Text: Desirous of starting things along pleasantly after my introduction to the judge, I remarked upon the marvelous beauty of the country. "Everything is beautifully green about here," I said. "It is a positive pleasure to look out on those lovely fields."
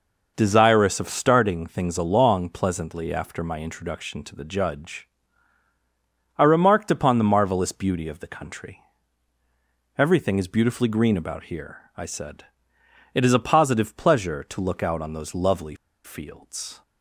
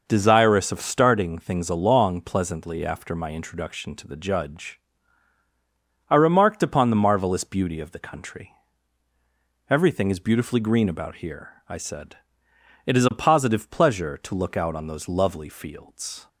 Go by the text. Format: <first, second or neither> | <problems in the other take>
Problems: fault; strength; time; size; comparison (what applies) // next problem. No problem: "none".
second | pauses between "lovely" and "fields"; slight; at 15.7 s; 0.28 s long